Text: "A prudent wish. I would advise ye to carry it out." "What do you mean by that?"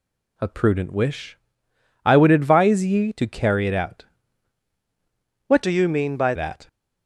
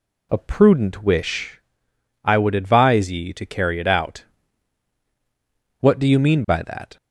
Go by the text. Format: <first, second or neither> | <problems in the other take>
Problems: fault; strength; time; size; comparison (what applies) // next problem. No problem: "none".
second | changes voice from "do" to "by"; from 5.6 to 6.3 s; 0.7 s long